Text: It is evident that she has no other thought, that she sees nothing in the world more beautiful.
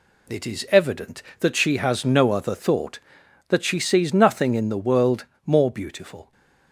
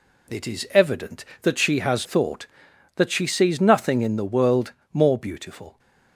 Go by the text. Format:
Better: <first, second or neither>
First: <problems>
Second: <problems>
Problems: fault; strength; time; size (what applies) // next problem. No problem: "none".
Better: first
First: pauses between "world" and "more"; slight; at 5.2 s; 0.20 s long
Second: skips "no other"; at 2.0 s // pauses between "world" and "more"; slight; at 4.7 s; 0.20 s long